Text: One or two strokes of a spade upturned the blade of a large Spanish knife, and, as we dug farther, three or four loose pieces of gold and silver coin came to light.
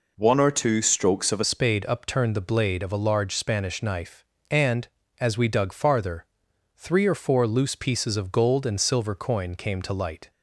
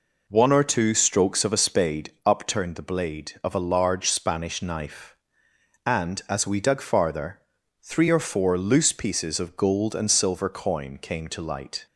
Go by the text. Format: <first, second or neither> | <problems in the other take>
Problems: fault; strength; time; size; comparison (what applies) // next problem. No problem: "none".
second | changes voice at "spade"; from 1.4 s on; 8.9 s long